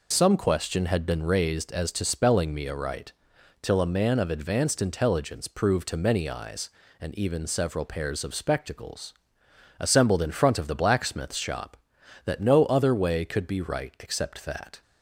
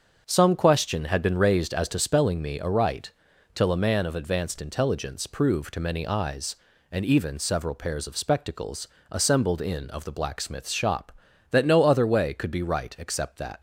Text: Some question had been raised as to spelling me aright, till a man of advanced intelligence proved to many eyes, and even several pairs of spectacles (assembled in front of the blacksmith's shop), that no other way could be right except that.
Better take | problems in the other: first | starts louder than the rest; until 1.2 s; 7 dB // skips "front"; at 9.9 s

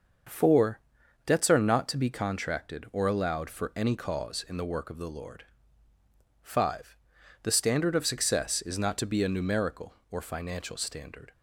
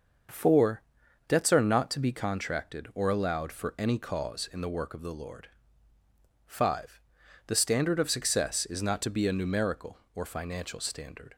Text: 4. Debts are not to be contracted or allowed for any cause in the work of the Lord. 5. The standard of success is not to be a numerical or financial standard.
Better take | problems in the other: neither | starts louder than the rest; the same in both

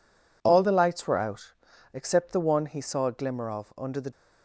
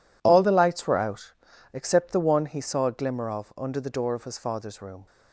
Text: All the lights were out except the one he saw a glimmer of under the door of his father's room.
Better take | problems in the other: second | pauses between "out" and "except"; at 1.5 s; 0.40 s long; also in the second // stops before "door of his father's room"; at 4.1 s

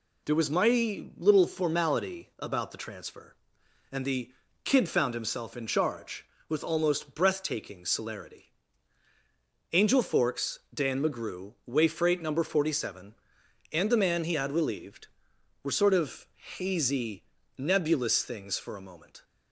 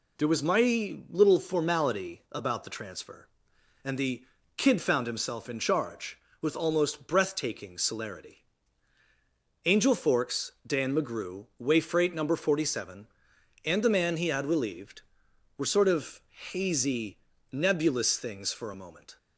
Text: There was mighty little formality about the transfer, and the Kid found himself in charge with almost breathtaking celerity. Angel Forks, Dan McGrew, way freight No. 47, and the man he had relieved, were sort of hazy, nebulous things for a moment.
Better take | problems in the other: neither | pauses between "the" and "Kid"; slight; the same in both // pauses between "of" and "hazy"; slight; the same in both

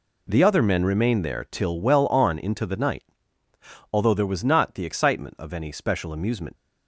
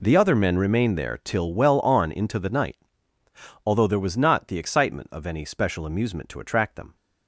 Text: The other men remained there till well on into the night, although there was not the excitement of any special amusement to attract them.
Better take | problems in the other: second | stops before "to attract them"; at 6.5 s

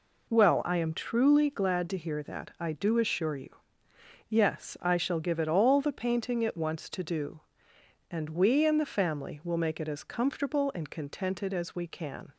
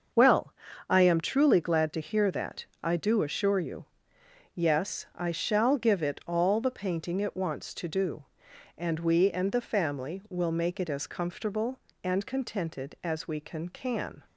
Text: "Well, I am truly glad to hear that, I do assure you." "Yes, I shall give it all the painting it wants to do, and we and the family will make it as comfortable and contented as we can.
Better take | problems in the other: first | starts louder than the rest; until 1.5 s; 6.5 dB // says "can" twice; at 13.6 s

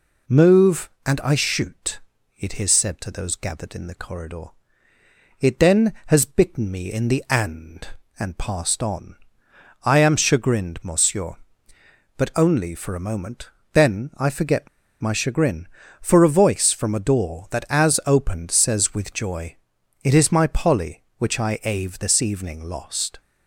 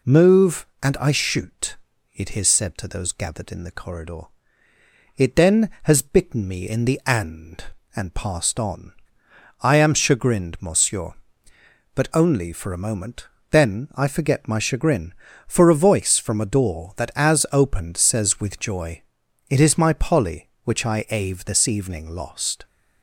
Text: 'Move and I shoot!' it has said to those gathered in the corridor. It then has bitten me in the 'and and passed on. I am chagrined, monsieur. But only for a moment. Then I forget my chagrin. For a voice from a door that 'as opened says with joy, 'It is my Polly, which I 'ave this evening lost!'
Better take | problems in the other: second | pauses between "forget" and "my"; slight; at 14.6 s; 0.33 s long

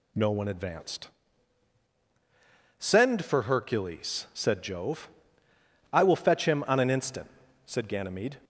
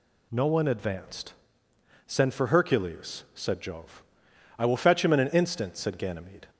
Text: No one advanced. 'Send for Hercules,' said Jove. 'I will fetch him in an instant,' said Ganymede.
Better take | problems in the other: second | says "on" for "in"; at 6.6 s

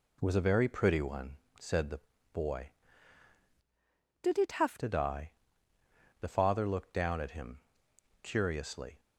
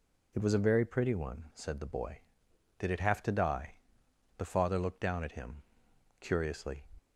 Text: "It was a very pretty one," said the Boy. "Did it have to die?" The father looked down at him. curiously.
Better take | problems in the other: second | pauses between "the" and "Boy"; slight; at 2.0 s; 0.32 s long // changes voice from "Did" to "have"; from 4.2 to 4.7 s; 0.5 s long

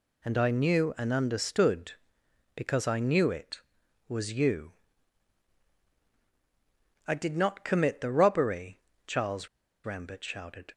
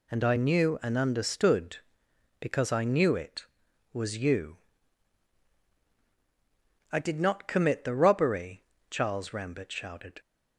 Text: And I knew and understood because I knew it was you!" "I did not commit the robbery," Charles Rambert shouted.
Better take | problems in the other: second | pauses between "Charles" and "Rambert"; slight; at 9.4 s; 0.36 s long

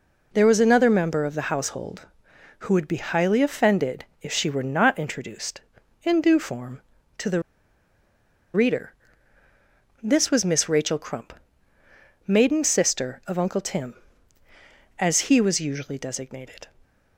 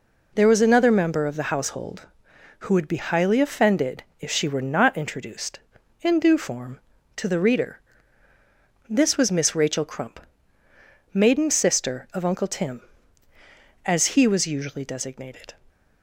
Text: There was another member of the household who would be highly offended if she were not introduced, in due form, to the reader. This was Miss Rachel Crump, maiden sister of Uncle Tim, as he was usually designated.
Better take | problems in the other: second | pauses between "offended" and "if"; slight; at 4.0 s; 0.16 s long; slight in the second // pauses between "the" and "reader"; at 7.4 s; 1.1 s long

